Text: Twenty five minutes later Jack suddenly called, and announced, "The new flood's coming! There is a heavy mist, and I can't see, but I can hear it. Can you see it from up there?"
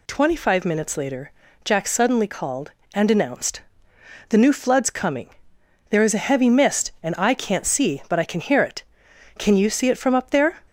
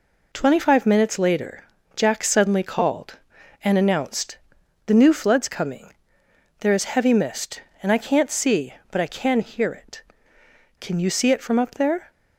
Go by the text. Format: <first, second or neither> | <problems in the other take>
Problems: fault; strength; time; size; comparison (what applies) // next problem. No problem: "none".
first | pauses between "later" and "Jack"; slight; at 1.6 s; 0.30 s long; slight in the first // skips "a"; at 6.8 s